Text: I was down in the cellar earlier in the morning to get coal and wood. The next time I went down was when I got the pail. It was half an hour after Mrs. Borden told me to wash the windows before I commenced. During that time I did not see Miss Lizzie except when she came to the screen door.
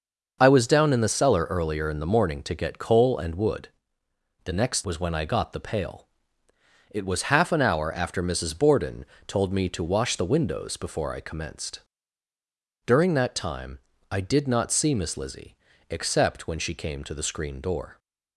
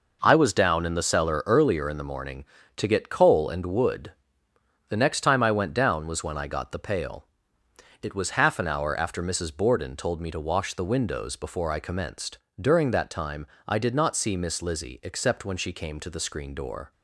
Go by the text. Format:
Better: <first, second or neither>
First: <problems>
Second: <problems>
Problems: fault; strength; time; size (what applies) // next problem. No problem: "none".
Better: second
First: starts louder than the rest; noticeable; until 1.4 s; 6 dB // skips "time I went down"; at 4.8 s // pauses between "Borden" and "told"; slight; at 9.0 s; 0.20 s long // pauses between "time" and "I"; slight; at 13.7 s; 0.32 s long // pauses between "Lizzie" and "except"; slight; at 15.5 s; 0.32 s long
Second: pauses between "time" and "I"; slight; at 13.4 s; 0.20 s long